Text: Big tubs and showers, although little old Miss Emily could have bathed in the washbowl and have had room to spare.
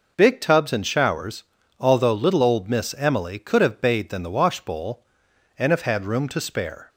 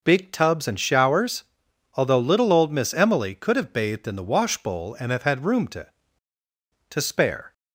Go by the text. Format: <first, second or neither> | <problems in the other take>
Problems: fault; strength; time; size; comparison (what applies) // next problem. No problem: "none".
first | says "to" twice; at 6.8 s